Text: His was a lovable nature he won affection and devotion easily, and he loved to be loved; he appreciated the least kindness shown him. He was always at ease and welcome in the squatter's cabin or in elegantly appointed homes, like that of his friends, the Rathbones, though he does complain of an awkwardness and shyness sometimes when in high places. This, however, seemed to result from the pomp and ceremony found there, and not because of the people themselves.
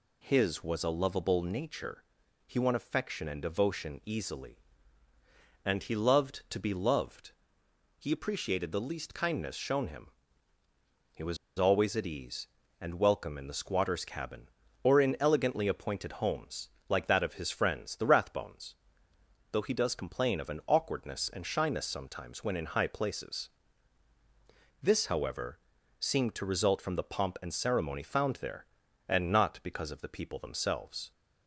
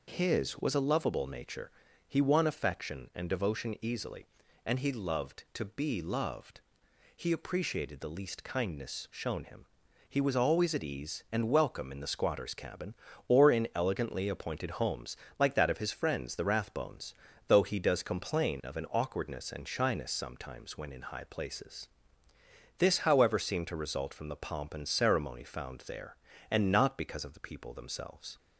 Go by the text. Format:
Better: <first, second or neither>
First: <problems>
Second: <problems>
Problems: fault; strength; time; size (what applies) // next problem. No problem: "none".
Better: second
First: pauses between "nature" and "he"; at 2.0 s; 0.42 s long // pauses between "was" and "always"; slight; at 11.3 s; 0.21 s long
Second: pauses between "nature" and "he"; slight; at 1.7 s; 0.36 s long